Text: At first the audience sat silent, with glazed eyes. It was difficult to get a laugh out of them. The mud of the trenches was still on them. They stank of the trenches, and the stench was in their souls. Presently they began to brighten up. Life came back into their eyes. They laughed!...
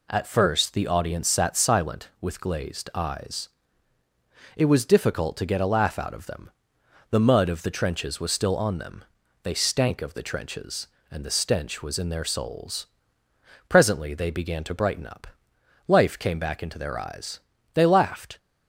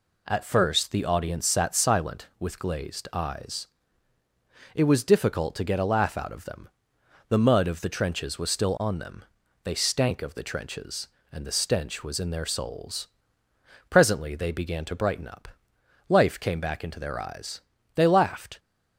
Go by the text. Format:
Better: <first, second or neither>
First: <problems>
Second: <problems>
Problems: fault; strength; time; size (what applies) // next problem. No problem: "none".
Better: neither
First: none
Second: none